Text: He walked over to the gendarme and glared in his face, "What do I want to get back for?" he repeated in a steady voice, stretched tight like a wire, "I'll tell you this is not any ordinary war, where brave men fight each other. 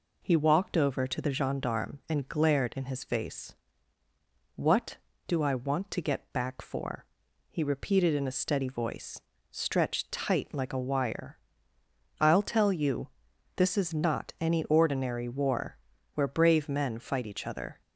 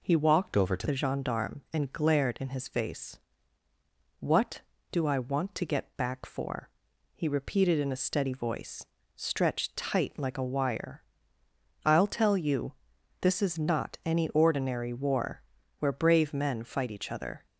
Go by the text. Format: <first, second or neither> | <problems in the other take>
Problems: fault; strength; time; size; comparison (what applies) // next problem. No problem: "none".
first | changes voice from "over" to "to"; from 0.5 to 0.8 s; 0.3 s long // pauses between "you" and "this"; noticeable; at 12.7 s; 0.48 s long; noticeable in the first